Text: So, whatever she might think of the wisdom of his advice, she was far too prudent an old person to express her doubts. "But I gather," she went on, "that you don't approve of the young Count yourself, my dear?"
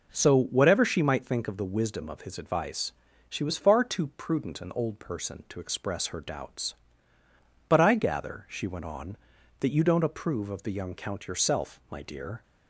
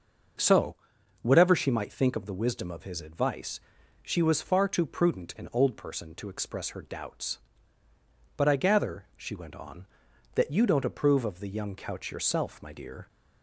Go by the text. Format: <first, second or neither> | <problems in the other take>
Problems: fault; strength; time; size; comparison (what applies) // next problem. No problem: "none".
first | starts louder than the rest; noticeable; until 1.8 s; 6 dB // says "Couch" for "Count"; at 11.7 s